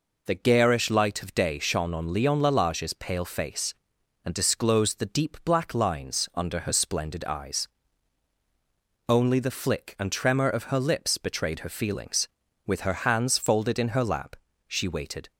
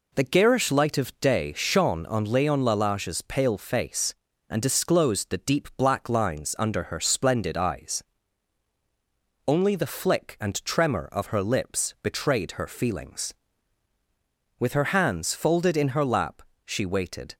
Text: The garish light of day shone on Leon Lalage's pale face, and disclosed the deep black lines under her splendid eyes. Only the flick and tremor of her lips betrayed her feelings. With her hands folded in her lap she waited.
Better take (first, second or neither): neither